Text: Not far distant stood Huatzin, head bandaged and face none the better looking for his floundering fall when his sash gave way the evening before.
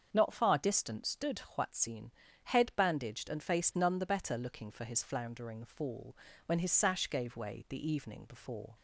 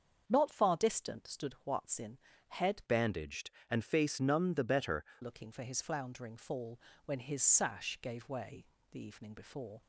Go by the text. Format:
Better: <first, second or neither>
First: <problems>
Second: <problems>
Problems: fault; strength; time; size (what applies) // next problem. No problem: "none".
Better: first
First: starts louder than the rest; until 1.1 s; 7 dB // pauses between "fall" and "when"; slight; at 6.1 s; 0.30 s long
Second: starts louder than the rest; until 1.2 s; 7 dB // changes voice from "bandaged" to "better"; from 2.8 to 5.0 s; 2.2 s long // pauses between "fall" and "when"; slight; at 6.7 s; 0.28 s long // pauses between "way" and "the"; slight; at 8.6 s; 0.26 s long